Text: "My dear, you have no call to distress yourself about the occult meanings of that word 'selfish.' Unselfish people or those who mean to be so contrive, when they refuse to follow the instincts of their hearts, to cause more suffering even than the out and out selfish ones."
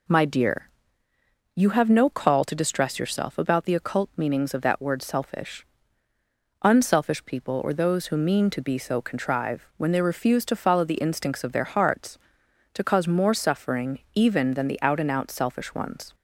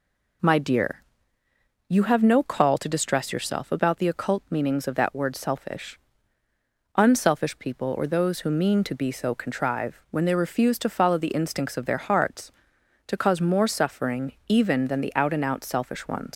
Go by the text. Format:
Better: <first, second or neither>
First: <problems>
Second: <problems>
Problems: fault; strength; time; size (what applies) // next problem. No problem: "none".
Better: first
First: pauses between "suffering" and "even"; slight; at 13.9 s; 0.16 s long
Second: pauses between "suffering" and "even"; slight; at 14.3 s; 0.16 s long // leaves "ones" unfinished; at 16.3 s; 125 ms